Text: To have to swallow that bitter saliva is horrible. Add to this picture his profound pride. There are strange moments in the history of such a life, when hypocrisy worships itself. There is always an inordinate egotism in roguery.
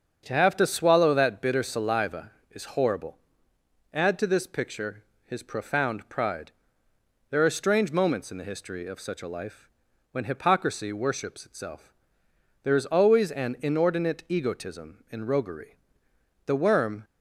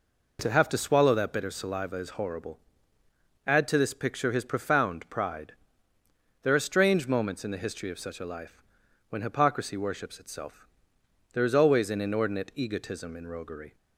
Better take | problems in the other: second | starts louder than the rest; until 1.2 s; 7 dB // pauses between "picture" and "his"; slight; at 5.0 s; 0.22 s long // goes on to say "The worm"; from 16.4 s on; 0.58 s long

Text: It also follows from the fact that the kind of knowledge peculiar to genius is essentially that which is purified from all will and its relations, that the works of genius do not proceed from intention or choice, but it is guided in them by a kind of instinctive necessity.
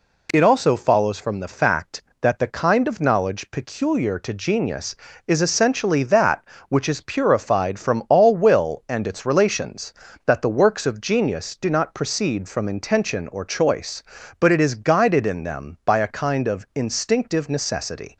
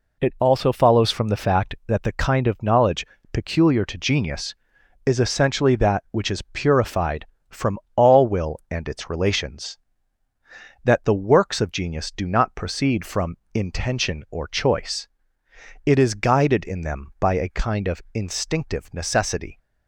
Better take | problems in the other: first | pauses between "knowledge" and "peculiar"; slight; at 3.0 s; 0.28 s long // pauses between "from" and "all"; slight; at 7.7 s; 0.18 s long // pauses between "from" and "intention"; slight; at 13.3 s; 0.18 s long // skips "but"; at 15.4 s

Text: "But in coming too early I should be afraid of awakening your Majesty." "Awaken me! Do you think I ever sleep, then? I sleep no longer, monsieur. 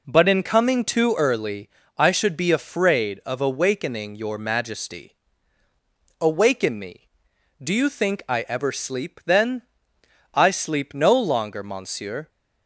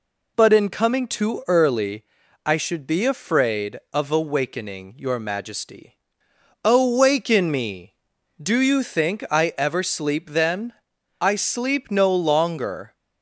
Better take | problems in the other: first | pauses between "early" and "I"; at 2.0 s; 0.42 s long; slight in the first // stops before "monsieur"; at 12.9 s

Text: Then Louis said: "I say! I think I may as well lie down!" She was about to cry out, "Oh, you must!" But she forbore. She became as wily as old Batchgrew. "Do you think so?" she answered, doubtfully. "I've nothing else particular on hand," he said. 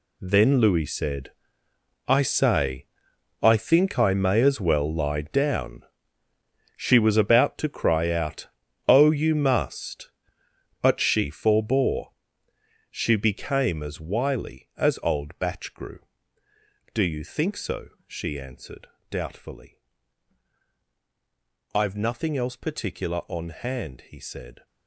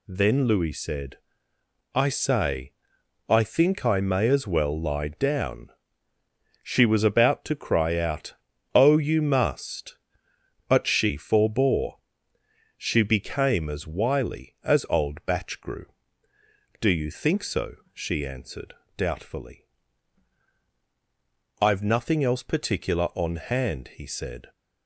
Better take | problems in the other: second | gets quieter; strong; throughout; 12.5 dB

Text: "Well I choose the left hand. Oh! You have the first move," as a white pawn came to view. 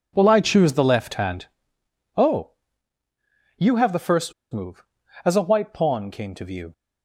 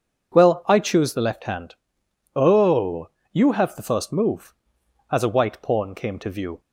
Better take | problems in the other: second | pauses between "first" and "move"; slight; at 4.3 s; 0.21 s long

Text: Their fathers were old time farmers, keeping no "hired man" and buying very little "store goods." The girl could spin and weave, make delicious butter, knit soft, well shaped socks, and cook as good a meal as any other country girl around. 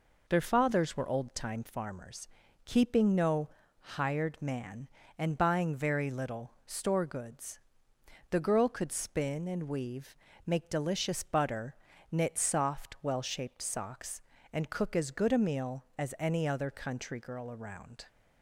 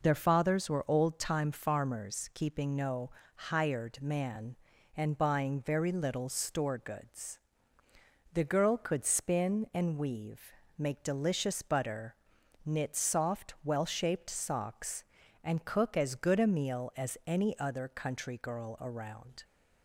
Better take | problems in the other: neither | pauses between "no" and "hired"; slight; the same in both

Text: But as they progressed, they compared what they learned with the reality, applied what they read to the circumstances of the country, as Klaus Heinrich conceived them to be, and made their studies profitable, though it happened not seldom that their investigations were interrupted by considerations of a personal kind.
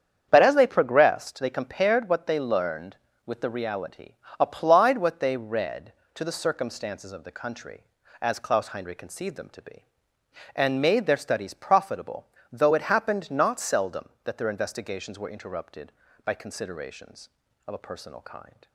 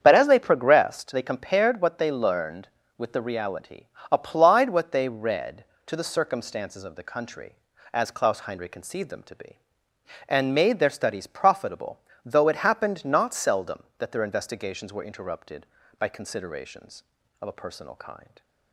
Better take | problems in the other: neither | starts louder than the rest; strong; the same in both

